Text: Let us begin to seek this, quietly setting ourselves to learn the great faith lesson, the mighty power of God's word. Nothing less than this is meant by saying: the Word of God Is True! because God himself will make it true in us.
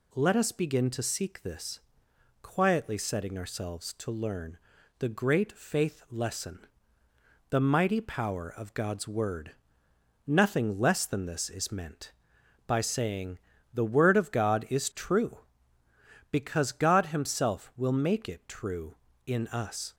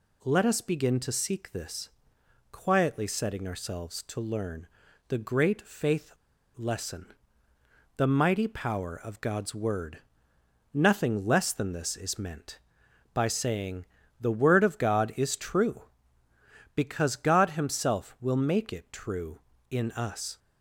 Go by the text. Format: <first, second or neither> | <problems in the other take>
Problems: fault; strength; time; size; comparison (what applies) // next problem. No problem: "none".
first | pauses between "learn" and "the"; at 4.6 s; 0.40 s long; also in the first // pauses between "faith" and "lesson"; at 6.1 s; 0.45 s long